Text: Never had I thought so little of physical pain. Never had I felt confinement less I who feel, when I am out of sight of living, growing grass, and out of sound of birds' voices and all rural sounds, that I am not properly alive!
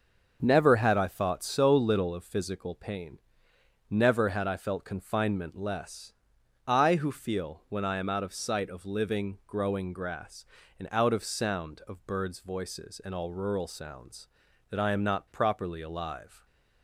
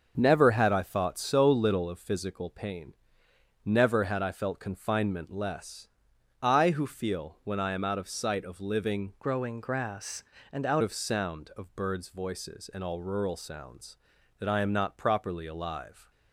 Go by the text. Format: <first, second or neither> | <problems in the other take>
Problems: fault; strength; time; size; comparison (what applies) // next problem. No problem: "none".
first | starts louder than the rest; until 1.1 s; 6.5 dB; also in the first // pauses between "less" and "I"; noticeable; at 5.8 s; 0.54 s long; noticeable in the first // changes voice from "growing" to "out"; from 9.2 to 10.8 s; 1.6 s long